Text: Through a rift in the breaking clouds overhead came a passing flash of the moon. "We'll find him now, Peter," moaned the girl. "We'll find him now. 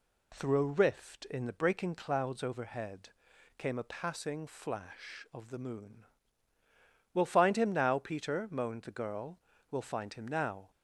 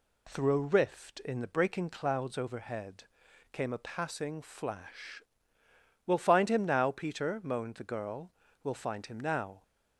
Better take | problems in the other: first | pauses between "overhead" and "came"; noticeable; at 3.0 s; 0.50 s long; noticeable in the first // skips "of the moon"; at 5.6 s

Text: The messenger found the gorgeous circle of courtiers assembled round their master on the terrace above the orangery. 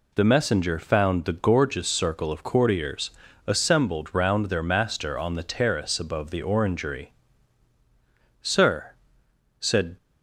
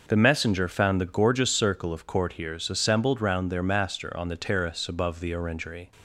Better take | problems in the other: second | pauses between "courtiers" and "assembled"; slight; at 3.1 s; 0.36 s long // goes on to say "Sir said"; from 8.4 s on; 1.5 s long

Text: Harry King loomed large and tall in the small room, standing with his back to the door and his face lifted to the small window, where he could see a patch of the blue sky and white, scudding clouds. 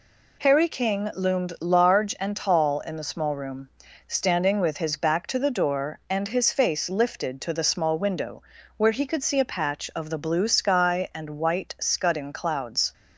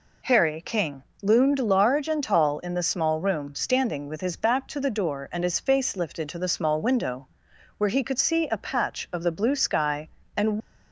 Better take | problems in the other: first | pauses between "King" and "loomed"; slight; at 1.0 s; 0.20 s long // stops before "white scudding clouds"; at 10.6 s

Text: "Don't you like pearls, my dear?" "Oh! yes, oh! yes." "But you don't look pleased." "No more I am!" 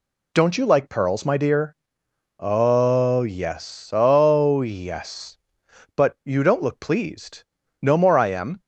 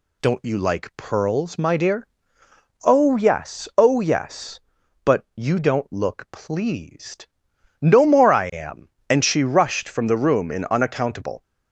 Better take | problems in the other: first | goes on to say "And she rushed from the room in unaccountable"; strong; from 9.0 s on; 2.3 s long

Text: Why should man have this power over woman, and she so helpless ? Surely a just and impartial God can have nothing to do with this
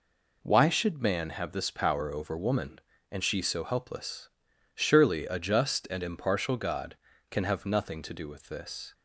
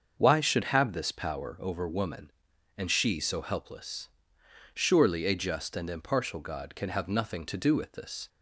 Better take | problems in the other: first | starts louder than the rest; until 1.1 s; 6.5 dB // skips "man"; at 0.6 s

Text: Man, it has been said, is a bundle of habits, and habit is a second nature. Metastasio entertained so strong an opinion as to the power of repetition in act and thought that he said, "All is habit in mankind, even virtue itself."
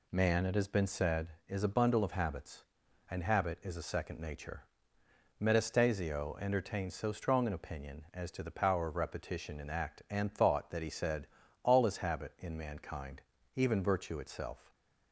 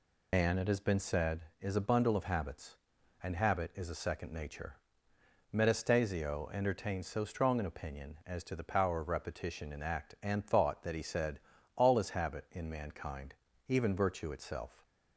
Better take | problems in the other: first | loses the start of "Man"; at 0.3 s; 105 ms

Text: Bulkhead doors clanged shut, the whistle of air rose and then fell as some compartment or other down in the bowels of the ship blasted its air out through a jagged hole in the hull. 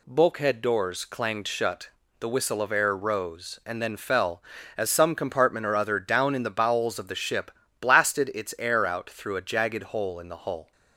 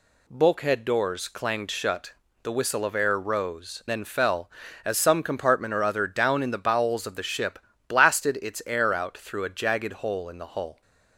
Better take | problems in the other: first | skips "and"; at 3.8 s // pauses between "ship" and "blasted"; slight; at 7.5 s; 0.28 s long; slight in the first

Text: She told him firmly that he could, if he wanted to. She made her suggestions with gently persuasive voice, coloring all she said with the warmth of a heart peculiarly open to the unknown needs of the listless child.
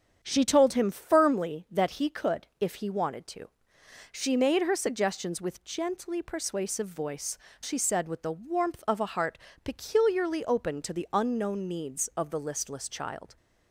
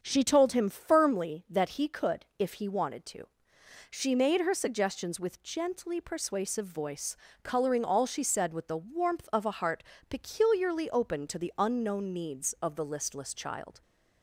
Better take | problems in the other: second | starts louder than the rest; strong; until 1.2 s; 7.5 dB; also in the second // skips "coloring all"; at 7.4 s // pauses between "heart" and "peculiarly"; slight; at 9.3 s; 0.26 s long; slight in the second

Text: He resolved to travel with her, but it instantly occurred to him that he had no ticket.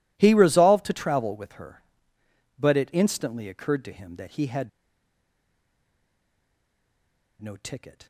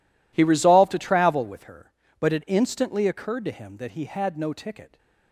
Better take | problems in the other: second | pauses between "had" and "no"; strong; at 4.6 s; 2.7 s long

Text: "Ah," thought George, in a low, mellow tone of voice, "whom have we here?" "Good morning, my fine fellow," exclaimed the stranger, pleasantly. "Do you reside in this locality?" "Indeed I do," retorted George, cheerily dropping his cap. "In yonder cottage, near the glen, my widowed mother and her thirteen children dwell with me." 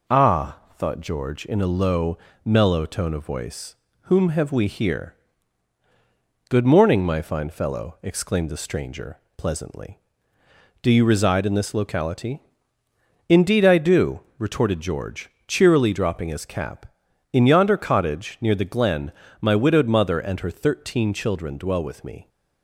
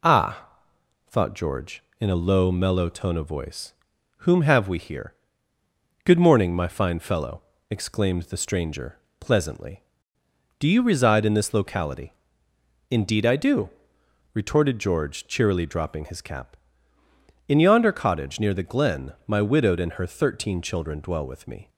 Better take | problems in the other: first | skips "mother"; at 19.7 s

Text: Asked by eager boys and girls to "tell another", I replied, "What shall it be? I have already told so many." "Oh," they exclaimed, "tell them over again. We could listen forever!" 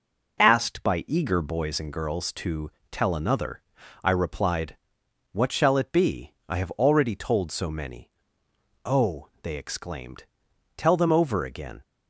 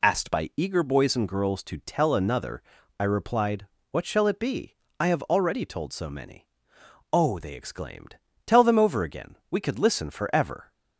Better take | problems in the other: second | pauses between "to" and "tell"; slight; at 2.7 s; 0.22 s long // stops before "We could listen forever"; at 11.8 s

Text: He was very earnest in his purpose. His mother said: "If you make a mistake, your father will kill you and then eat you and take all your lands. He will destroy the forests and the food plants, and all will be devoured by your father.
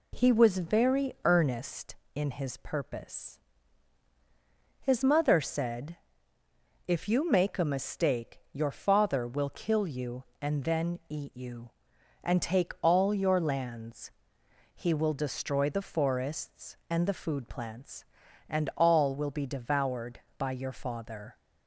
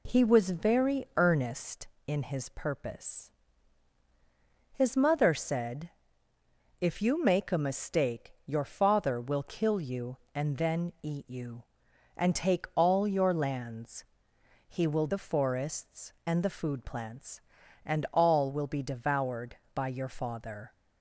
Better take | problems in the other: first | skips "destroy"; at 15.0 s

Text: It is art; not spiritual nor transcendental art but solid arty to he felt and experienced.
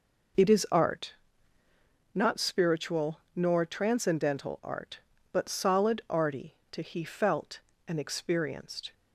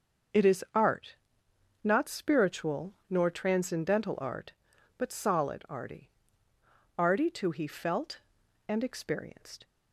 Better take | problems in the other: first | starts louder than the rest; until 2.1 s; 6.5 dB // says "arty" twice; at 6.9 s

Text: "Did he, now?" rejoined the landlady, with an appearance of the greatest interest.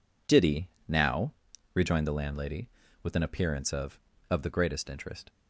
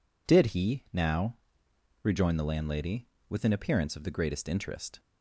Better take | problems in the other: second | says "of" twice; at 4.3 s

